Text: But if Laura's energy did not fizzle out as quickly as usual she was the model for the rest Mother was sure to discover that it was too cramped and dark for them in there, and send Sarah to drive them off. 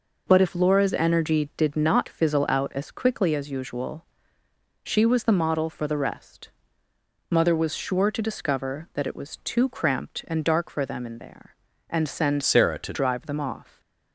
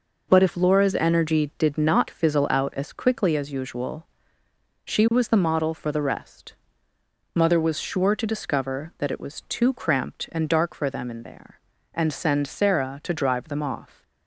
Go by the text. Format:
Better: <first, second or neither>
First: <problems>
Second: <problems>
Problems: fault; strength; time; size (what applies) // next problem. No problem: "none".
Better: second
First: pauses between "usual" and "she"; noticeable; at 4.0 s; 0.80 s long // pauses between "rest" and "Mother"; noticeable; at 6.4 s; 0.80 s long // changes voice from "Sarah" to "to"; from 12.4 to 12.9 s; 0.5 s long // stays silent after the last word; slight; from 13.6 s on; 0.5 s long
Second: pauses between "usual" and "she"; noticeable; at 4.0 s; 0.80 s long // pauses between "rest" and "Mother"; noticeable; at 6.5 s; 0.80 s long